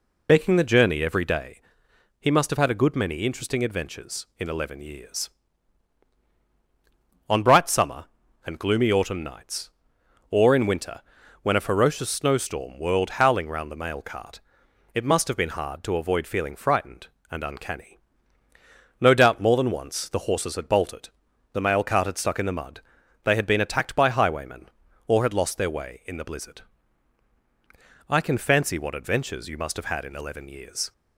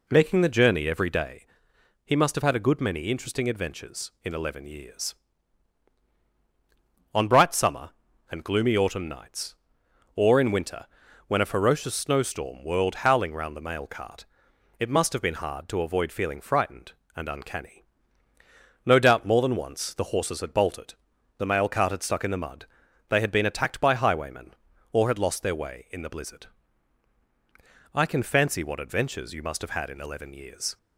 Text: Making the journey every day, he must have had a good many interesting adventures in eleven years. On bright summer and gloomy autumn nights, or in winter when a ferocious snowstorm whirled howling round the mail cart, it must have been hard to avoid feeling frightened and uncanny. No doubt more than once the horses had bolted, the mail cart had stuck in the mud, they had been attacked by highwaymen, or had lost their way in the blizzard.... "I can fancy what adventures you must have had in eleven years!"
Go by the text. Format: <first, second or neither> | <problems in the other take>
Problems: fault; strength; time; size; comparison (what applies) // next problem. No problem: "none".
second | loses the start of "Making"; at 0.2 s; 55 ms // pauses between "winter" and "when"; at 11.0 s; 0.42 s long; also in the second